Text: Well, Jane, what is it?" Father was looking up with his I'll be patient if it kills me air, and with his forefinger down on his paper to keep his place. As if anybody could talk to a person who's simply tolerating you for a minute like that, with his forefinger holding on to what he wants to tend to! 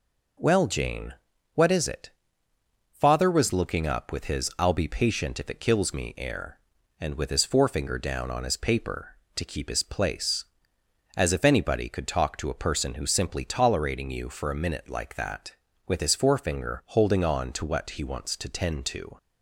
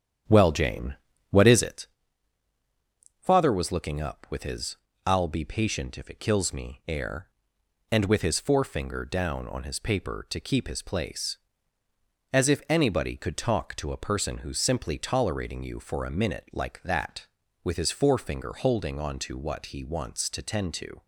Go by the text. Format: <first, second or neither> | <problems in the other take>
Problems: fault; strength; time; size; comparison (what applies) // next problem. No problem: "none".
first | starts louder than the rest; strong; until 1.8 s; 9 dB // pauses between "his" and "I'll"; slight; at 4.7 s; 0.30 s long